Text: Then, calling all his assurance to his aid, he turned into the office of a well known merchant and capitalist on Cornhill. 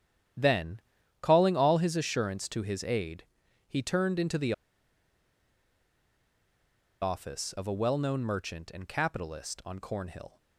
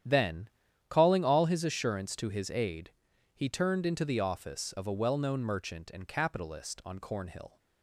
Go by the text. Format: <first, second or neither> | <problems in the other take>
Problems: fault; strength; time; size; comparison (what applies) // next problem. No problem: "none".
second | starts louder than the rest; strong; until 1.7 s; 10 dB; strong in the second // pauses between "the" and "office"; strong; at 4.5 s; 2.4 s long